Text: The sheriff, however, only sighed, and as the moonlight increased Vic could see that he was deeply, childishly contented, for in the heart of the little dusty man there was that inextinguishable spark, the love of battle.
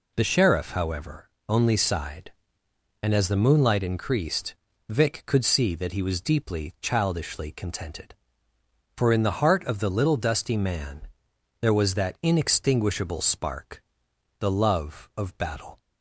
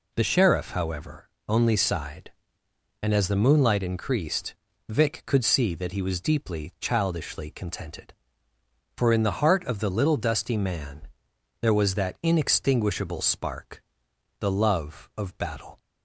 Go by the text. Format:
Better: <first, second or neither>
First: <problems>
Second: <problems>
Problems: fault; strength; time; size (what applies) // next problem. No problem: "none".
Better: neither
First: pauses between "increased" and "Vic"; slight; at 4.5 s; 0.34 s long // pauses between "man" and "there"; noticeable; at 11.0 s; 0.54 s long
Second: pauses between "increased" and "Vic"; slight; at 4.5 s; 0.34 s long // pauses between "man" and "there"; noticeable; at 11.0 s; 0.54 s long